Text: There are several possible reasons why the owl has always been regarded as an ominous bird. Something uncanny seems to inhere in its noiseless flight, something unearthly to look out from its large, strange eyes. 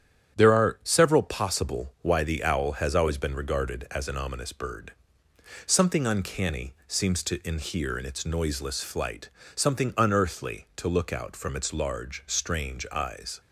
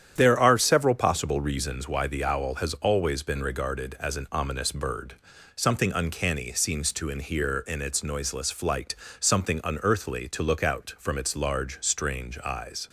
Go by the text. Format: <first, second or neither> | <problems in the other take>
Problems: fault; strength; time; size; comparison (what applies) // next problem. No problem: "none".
second | starts louder than the rest; strong; until 1.4 s; 9 dB; strong in the second // skips "reasons"; at 1.9 s